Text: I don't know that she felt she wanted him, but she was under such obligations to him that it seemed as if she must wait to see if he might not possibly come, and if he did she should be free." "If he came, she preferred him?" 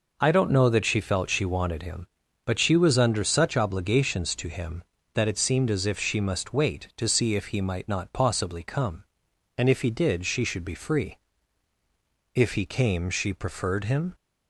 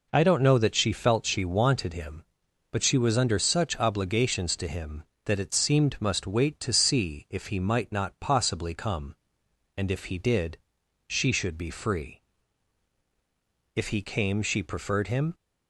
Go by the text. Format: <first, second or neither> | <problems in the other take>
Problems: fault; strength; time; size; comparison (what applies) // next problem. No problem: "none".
first | skips "as if she"; at 6.0 s // pauses between "did" and "she"; noticeable; at 10.5 s; 0.52 s long